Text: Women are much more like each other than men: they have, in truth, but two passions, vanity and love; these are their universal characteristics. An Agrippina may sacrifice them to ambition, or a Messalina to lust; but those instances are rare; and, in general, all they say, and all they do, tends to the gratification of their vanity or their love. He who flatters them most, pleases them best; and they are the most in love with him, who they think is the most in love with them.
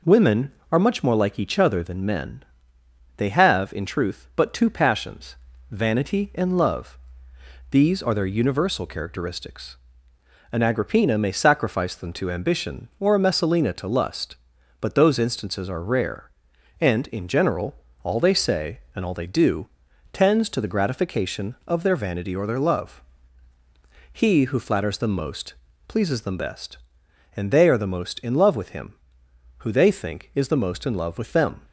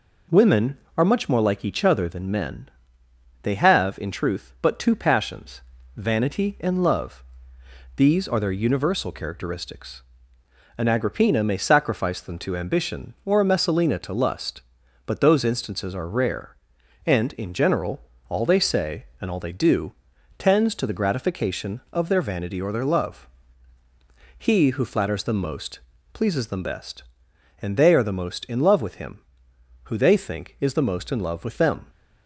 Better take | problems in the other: neither | none

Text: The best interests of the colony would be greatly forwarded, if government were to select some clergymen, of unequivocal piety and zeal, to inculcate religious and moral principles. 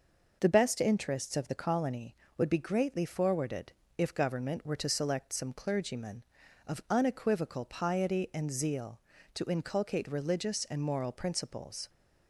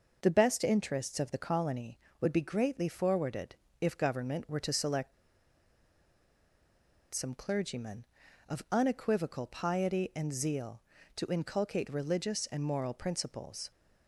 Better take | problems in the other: first | pauses between "select" and "some"; strong; at 5.1 s; 1.9 s long

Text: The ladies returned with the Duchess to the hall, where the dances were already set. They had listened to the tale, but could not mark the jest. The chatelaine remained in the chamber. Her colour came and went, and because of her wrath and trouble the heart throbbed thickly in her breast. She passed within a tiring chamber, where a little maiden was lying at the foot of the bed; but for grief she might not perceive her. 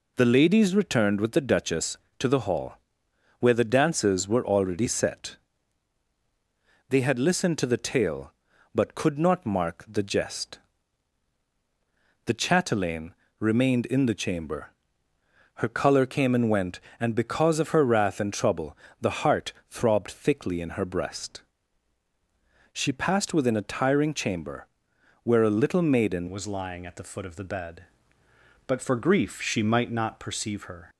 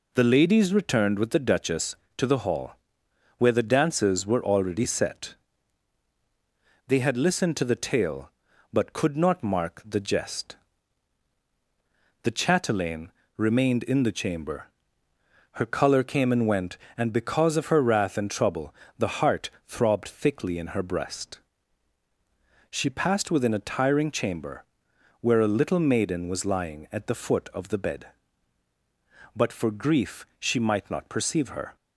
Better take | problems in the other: second | pauses between "chatelaine" and "remained"; slight; at 13.1 s; 0.28 s long; slight in the second // pauses between "trouble" and "the"; slight; at 18.7 s; 0.22 s long; slight in the second // pauses between "heart" and "throbbed"; slight; at 19.5 s; 0.16 s long; slight in the second // changes voice at "was"; from 26.2 s on; 4.6 s long

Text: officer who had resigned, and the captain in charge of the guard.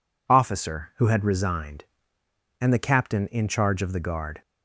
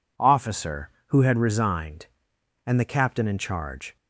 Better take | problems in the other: first | stops before "of the guard"; at 3.9 s

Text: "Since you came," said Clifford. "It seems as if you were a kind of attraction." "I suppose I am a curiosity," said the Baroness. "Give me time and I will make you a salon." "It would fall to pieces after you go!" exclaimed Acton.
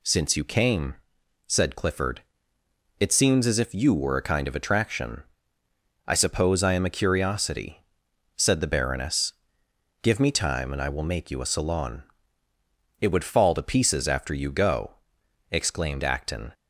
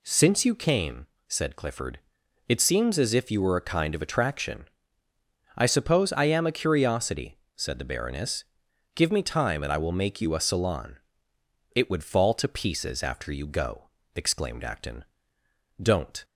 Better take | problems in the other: first | goes on to say "Don't"; slight; from 15.8 s on; 0.44 s long

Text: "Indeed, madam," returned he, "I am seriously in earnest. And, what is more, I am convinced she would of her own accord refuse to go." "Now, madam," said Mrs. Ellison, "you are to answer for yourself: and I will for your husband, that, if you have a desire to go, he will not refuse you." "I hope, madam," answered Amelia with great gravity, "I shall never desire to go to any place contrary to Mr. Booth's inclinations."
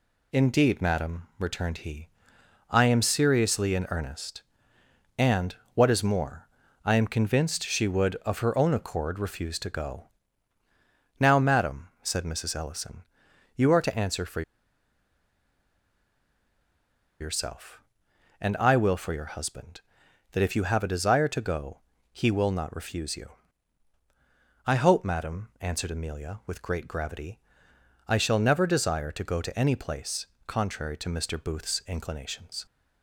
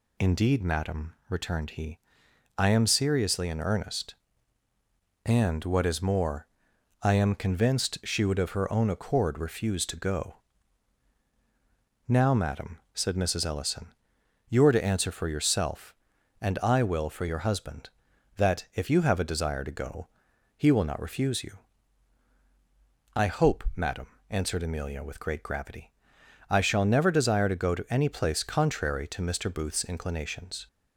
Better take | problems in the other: second | pauses between "for" and "yourself"; strong; at 14.4 s; 2.7 s long // pauses between "place" and "contrary"; slight; at 30.2 s; 0.20 s long

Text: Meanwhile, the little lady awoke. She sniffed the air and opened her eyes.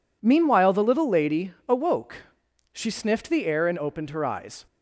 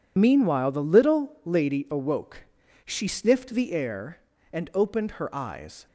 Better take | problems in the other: first | loses the start of "Meanwhile"; at 0.1 s; 45 ms

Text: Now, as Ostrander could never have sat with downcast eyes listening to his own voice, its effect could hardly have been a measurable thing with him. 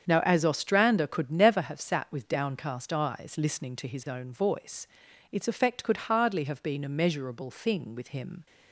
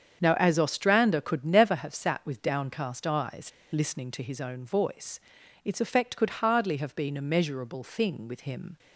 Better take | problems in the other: first | starts louder than the rest; strong; until 1.2 s; 7.5 dB; strong in the first // pauses between "eyes" and "listening"; slight; at 3.4 s; 0.23 s long

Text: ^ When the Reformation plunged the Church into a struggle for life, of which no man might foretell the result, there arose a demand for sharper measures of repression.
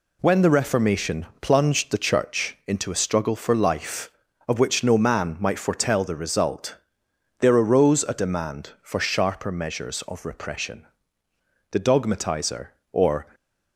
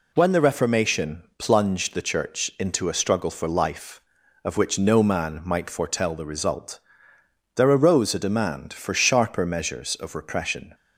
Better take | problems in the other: second | pauses between "Reformation" and "plunged"; slight; at 1.2 s; 0.16 s long; slight in the second // goes on to say "The dogmatizer or"; from 11.7 s on; 1.6 s long

